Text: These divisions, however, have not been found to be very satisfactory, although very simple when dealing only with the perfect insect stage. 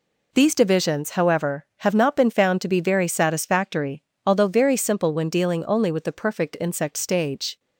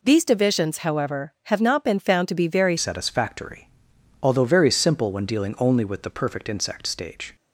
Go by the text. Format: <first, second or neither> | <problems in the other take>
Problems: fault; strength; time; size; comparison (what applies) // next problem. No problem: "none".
first | changes voice at "satisfactory"; from 2.7 s on; 4.6 s long